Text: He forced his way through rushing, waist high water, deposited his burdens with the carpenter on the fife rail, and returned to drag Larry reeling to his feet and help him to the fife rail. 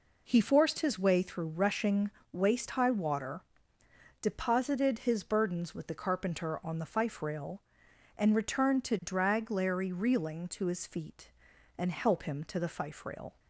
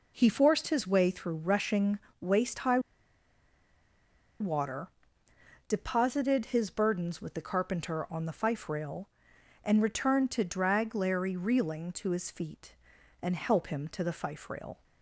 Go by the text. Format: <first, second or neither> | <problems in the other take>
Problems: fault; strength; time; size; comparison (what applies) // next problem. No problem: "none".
first | pauses between "high" and "water"; strong; at 2.7 s; 1.6 s long